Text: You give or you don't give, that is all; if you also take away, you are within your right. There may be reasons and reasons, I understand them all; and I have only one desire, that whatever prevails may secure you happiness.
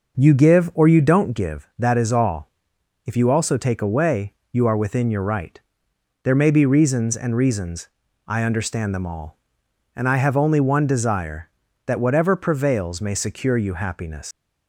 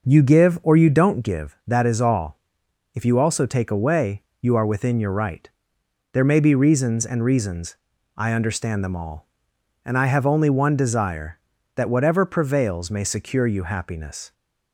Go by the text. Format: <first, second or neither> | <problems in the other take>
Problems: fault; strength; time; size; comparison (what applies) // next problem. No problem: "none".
second | leaves "happiness" unfinished; at 14.3 s; 125 ms